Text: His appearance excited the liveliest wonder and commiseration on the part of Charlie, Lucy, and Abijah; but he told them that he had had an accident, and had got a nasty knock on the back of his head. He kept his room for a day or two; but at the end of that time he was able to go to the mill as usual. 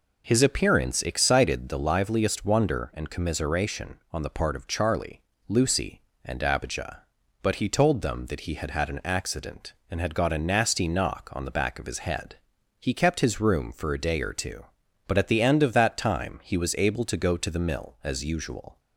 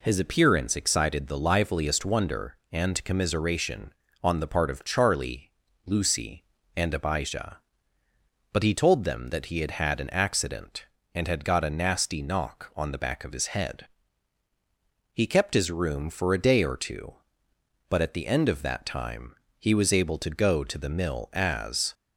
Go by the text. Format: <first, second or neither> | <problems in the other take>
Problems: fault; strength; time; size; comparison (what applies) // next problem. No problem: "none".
first | pauses between "time" and "he"; slight; at 19.3 s; 0.24 s long // stops before "usual"; at 21.9 s